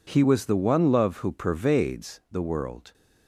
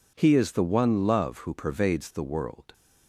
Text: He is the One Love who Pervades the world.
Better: second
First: says "was" for "is"; at 0.2 s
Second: none

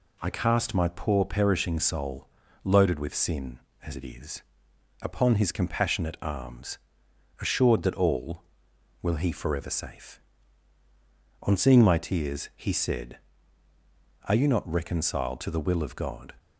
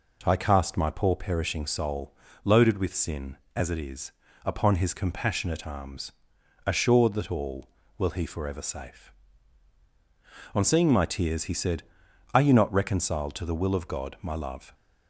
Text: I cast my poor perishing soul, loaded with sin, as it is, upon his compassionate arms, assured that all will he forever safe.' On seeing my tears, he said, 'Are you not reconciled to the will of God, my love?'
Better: second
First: stops before "my love"; at 16.3 s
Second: none

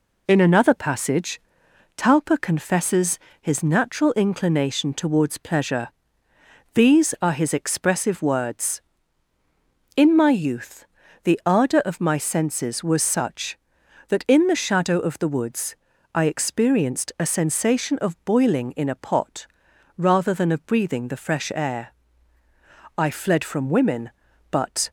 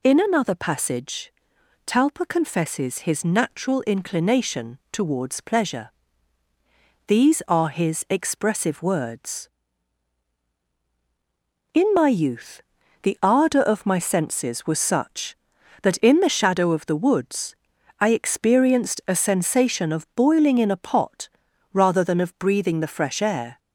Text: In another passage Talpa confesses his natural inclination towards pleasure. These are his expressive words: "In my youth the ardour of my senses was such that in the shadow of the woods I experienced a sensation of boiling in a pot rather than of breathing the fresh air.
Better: second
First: pauses between "passage" and "Talpa"; noticeable; at 1.3 s; 0.58 s long // pauses between "confesses" and "his"; slight; at 3.1 s; 0.22 s long // pauses between "youth" and "the"; at 10.8 s; 0.38 s long // pauses between "woods" and "I"; slight; at 15.7 s; 0.36 s long // pauses between "pot" and "rather"; noticeable; at 19.4 s; 0.50 s long // goes on to say "I fled from women but"; strong; from 22.9 s on; 1.9 s long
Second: pauses between "passage" and "Talpa"; noticeable; at 1.3 s; 0.52 s long // pauses between "youth" and "the"; at 12.6 s; 0.40 s long // pauses between "woods" and "I"; at 17.5 s; 0.42 s long // pauses between "pot" and "rather"; noticeable; at 21.2 s; 0.46 s long

